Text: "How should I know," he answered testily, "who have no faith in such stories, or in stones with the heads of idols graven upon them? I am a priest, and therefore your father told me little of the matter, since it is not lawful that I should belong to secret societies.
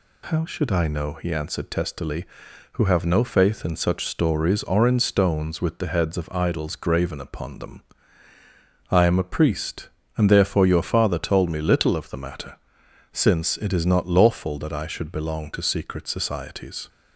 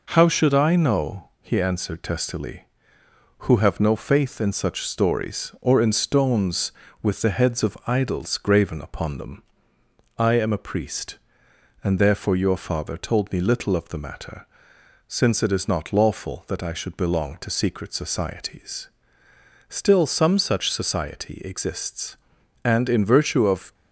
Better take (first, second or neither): first